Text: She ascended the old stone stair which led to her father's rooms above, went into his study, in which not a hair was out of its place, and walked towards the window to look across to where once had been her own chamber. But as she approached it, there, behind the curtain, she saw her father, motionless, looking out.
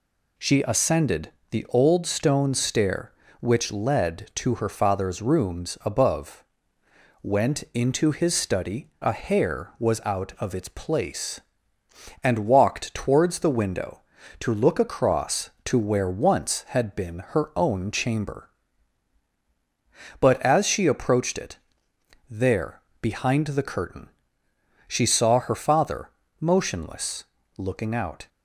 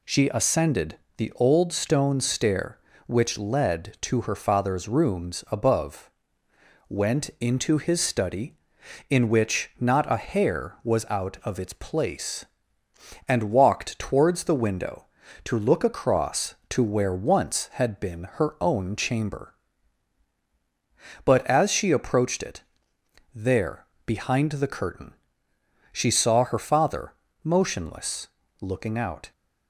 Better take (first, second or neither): second